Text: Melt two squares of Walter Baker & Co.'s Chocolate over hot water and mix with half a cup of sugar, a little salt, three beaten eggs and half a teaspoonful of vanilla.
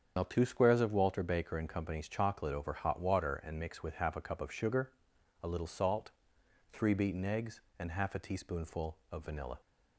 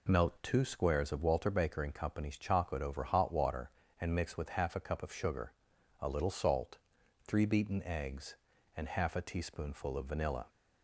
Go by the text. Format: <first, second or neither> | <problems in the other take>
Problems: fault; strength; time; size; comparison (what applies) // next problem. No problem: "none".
second | loses the start of "Melt"; at 0.1 s; 85 ms // starts louder than the rest; strong; until 1.1 s; 7.5 dB